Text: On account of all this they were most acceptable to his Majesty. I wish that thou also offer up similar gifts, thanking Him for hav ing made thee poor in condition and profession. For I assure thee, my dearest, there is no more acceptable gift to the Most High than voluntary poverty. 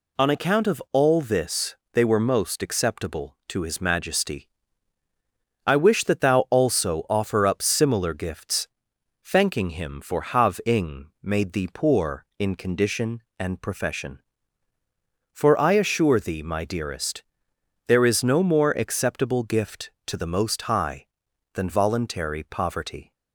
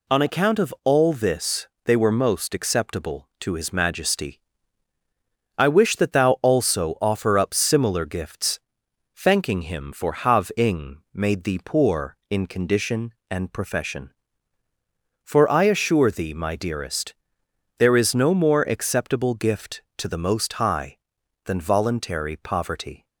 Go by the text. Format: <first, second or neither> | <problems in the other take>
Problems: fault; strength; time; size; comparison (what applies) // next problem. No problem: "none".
neither | pauses between "this" and "they"; slight; the same in both